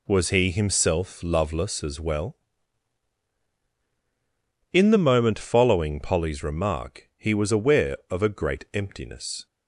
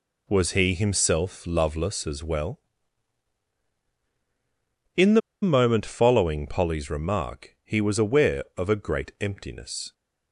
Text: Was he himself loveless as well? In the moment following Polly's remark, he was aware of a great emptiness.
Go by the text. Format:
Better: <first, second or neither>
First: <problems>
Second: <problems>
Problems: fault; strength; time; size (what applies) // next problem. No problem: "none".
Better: first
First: none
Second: pauses between "the" and "moment"; slight; at 5.2 s; 0.22 s long